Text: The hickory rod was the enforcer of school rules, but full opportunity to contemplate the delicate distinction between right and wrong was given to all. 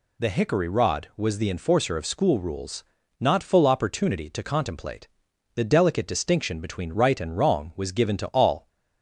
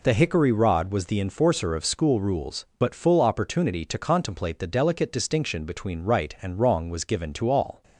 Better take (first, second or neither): second